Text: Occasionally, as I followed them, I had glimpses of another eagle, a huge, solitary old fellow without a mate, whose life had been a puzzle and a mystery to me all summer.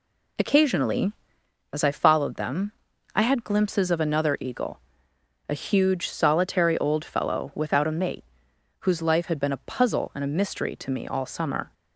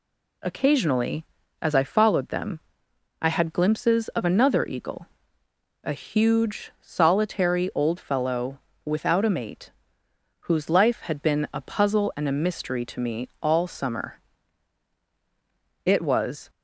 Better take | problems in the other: first | pauses between "fellow" and "without"; slight; at 8.5 s; 0.26 s long // goes on to say "It was"; noticeable; from 15.8 s on; 0.66 s long

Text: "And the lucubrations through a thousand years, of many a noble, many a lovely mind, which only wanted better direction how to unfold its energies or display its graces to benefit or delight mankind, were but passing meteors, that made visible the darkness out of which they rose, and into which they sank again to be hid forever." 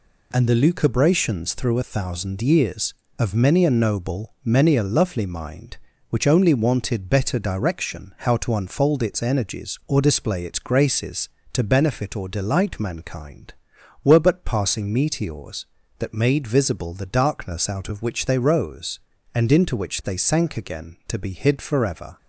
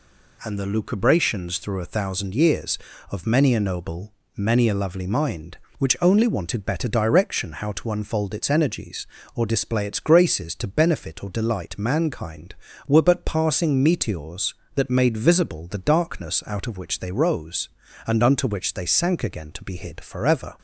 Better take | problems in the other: first | says "unto" for "into"; at 18.2 s

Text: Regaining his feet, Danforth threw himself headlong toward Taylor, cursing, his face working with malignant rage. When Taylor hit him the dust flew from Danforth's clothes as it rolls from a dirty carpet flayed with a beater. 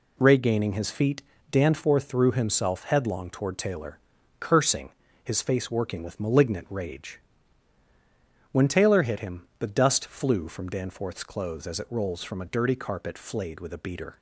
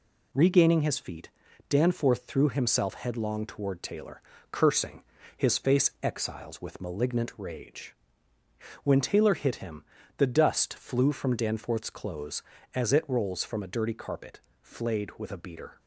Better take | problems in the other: first | says "exiles" for "working"; at 6.0 s // pauses between "him" and "the"; slight; at 9.8 s; 0.34 s long; slight in the first // pauses between "carpet" and "flayed"; slight; at 14.3 s; 0.24 s long

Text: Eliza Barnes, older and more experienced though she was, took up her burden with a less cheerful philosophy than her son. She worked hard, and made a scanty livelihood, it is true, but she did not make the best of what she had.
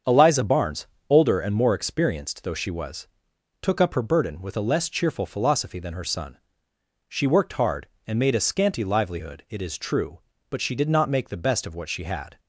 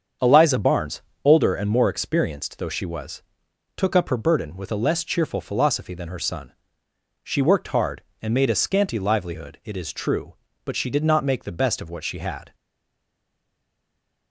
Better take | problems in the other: first | starts louder than the rest; strong; until 1.4 s; 7.5 dB; strong in the first // stays silent after the last word; noticeable; from 12.5 s on; 1.8 s long

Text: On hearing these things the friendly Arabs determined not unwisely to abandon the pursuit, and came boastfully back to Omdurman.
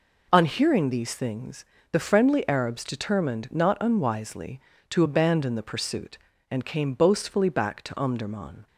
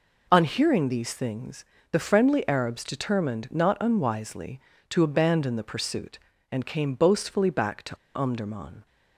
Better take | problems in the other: first | pauses between "things" and "the"; slight; at 1.6 s; 0.28 s long; slight in the first // pauses between "to" and "Omdurman"; slight; at 7.9 s; 0.17 s long

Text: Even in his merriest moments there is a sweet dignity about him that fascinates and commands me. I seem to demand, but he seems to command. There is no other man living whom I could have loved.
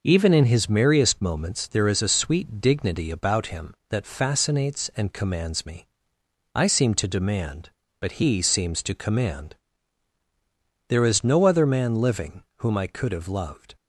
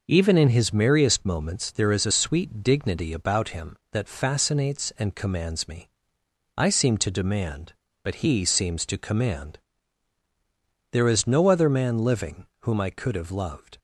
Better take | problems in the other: neither | none

